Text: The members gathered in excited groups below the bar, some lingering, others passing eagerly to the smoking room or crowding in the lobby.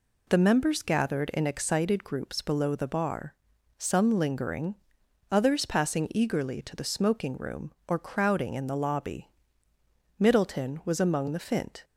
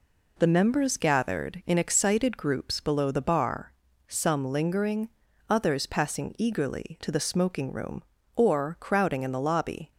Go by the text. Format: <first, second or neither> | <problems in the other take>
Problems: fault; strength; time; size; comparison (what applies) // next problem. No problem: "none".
second | goes on to say "Middleton was among the fint"; from 10.1 s on; 1.6 s long